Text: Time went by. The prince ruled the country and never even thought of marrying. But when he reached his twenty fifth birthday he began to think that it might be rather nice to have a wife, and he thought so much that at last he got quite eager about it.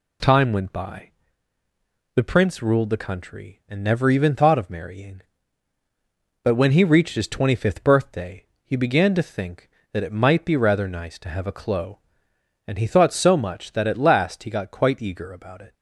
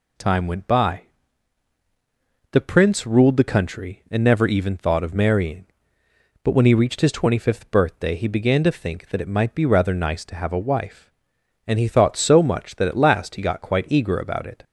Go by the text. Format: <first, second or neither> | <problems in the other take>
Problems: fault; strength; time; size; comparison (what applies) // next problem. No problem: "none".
second | pauses between "birthday" and "he"; slight; at 8.4 s; 0.18 s long // says "clo" for "wife"; at 11.5 s